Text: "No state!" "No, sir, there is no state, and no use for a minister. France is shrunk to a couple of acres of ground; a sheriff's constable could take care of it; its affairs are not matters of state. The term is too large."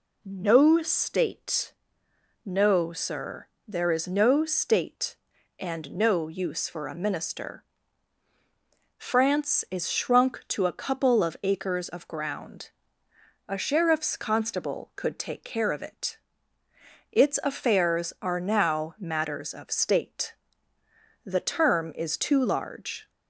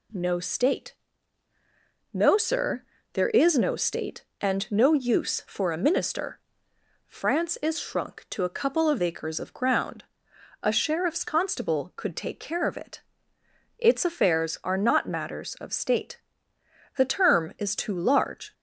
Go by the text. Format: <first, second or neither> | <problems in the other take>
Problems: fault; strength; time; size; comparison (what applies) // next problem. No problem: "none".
second | says "now" for "not"; at 18.3 s